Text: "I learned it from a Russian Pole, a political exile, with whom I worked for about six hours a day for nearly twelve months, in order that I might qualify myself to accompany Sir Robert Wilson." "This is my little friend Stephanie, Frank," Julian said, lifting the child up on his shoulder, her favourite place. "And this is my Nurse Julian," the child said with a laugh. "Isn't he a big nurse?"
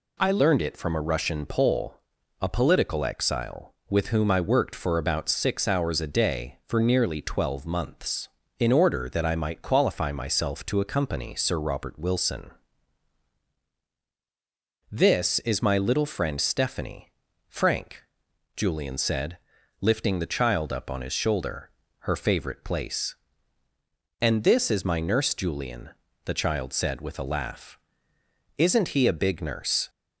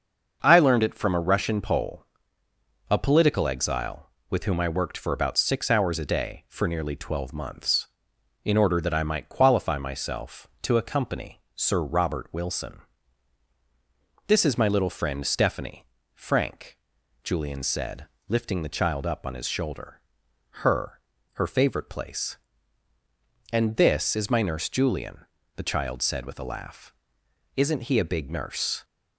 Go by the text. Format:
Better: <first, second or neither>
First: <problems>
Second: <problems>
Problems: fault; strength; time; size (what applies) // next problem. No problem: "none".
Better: first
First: none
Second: starts louder than the rest; until 1.4 s; 6.5 dB // says "her" twice; at 21.3 s